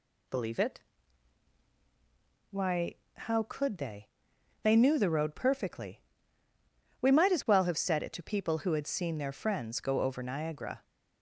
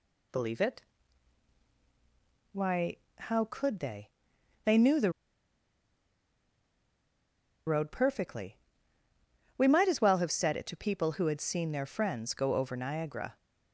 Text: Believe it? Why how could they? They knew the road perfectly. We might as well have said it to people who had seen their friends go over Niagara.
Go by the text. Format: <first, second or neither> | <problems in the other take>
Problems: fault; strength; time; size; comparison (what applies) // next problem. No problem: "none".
first | pauses between "Why" and "how"; slight; at 2.9 s; 0.20 s long; slight in the first // pauses between "the" and "road"; strong; at 5.1 s; 2.5 s long